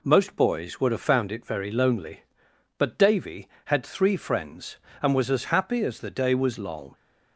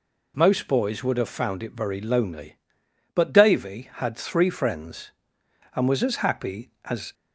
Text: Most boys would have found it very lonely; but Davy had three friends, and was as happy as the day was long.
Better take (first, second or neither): first